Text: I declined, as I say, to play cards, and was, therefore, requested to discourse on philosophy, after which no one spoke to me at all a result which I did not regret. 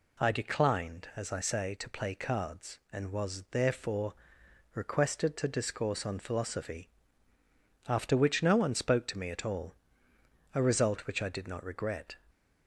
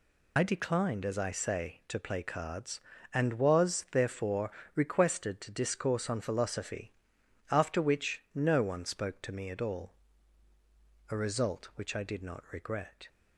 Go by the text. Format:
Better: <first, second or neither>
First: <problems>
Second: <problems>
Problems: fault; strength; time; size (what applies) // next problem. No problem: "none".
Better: first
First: pauses between "all" and "a"; noticeable; at 9.7 s; 0.80 s long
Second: loses the start of "I"; at 0.3 s; 50 ms // pauses between "all" and "a"; at 9.9 s; 1.2 s long